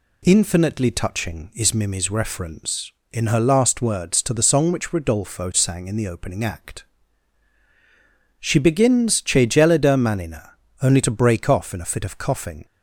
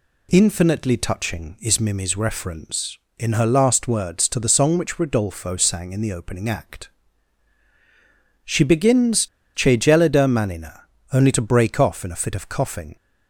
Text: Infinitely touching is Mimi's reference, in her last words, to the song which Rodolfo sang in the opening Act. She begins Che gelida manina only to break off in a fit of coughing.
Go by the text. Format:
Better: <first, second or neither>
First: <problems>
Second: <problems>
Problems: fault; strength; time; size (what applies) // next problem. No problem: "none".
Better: first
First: pauses between "manina" and "only"; slight; at 10.5 s; 0.28 s long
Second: pauses between "begins" and "Che"; slight; at 9.2 s; 0.28 s long // pauses between "manina" and "only"; slight; at 10.8 s; 0.28 s long